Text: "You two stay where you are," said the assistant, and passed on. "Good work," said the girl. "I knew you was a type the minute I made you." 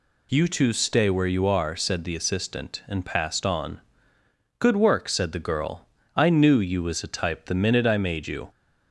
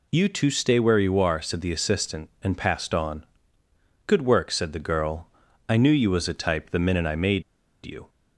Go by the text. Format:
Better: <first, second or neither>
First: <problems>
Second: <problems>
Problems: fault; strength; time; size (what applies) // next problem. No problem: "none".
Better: first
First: none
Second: pauses between "made" and "you"; at 7.4 s; 0.41 s long